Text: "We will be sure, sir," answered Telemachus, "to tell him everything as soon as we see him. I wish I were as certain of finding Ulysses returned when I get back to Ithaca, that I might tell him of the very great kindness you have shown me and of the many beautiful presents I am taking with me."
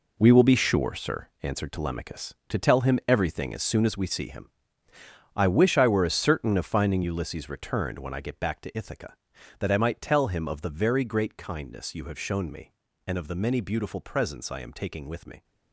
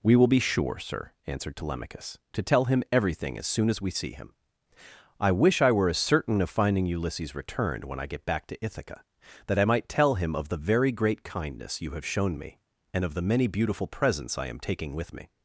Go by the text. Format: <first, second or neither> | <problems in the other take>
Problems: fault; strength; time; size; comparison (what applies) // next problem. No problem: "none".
second | gets quieter; strong; throughout; 10.5 dB